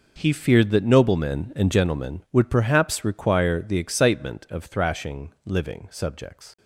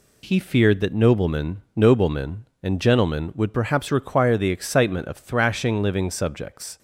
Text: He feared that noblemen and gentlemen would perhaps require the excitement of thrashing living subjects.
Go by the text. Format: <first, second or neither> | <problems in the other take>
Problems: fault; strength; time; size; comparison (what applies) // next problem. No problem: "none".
first | says "noblemen" twice; at 1.7 s